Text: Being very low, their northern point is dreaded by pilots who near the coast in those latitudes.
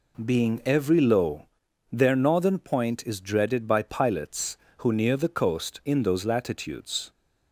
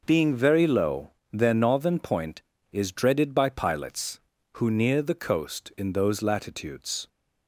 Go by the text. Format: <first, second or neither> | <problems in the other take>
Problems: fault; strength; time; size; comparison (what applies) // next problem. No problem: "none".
second | says "every" for "very"; at 0.6 s